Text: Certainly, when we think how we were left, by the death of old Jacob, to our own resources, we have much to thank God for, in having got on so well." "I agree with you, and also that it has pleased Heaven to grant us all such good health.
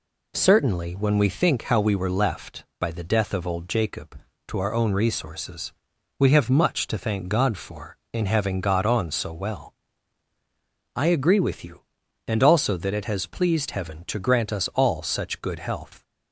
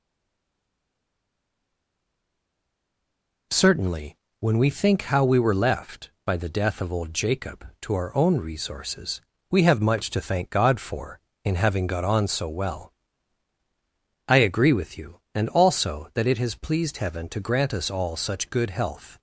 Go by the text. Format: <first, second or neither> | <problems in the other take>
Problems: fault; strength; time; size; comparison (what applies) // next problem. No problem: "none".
first | stays silent before the first word; strong; until 3.5 s; 3.5 s long